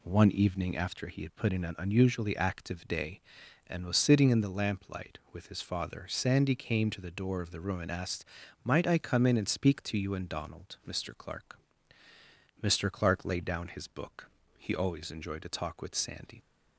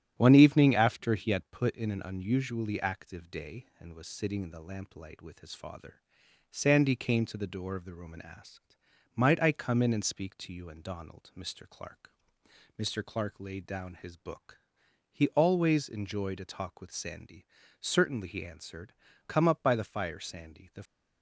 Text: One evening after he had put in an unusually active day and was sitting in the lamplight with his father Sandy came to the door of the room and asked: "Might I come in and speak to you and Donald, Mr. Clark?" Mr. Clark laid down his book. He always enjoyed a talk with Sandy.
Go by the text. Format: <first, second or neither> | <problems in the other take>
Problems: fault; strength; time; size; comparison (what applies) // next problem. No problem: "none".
first | starts louder than the rest; strong; until 1.1 s; 11.5 dB // pauses between "father" and "Sandy"; noticeable; at 6.0 s; 0.48 s long // goes on to say "Certainly he answered Come up by the fire Sandy The"; strong; from 17.7 s on; 3.0 s long